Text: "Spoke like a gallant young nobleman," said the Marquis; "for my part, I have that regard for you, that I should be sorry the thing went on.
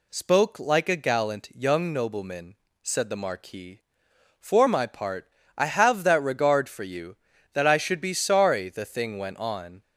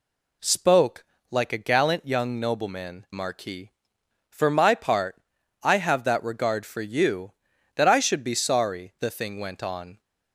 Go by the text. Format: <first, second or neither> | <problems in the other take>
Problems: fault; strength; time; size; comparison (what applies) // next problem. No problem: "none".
first | pauses between "Spoke" and "like"; slight; at 1.0 s; 0.26 s long // skips "said the"; at 3.0 s